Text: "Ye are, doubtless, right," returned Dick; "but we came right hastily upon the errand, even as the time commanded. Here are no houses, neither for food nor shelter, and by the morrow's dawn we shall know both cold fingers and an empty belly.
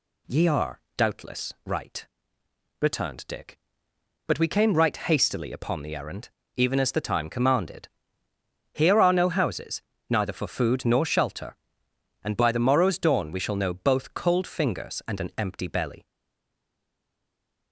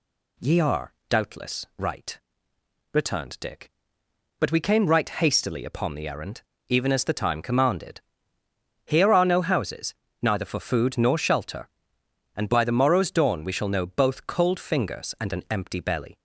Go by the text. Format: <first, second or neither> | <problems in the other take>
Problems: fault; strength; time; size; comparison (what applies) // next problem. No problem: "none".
second | stays silent after the last word; noticeable; from 16.0 s on; 1.7 s long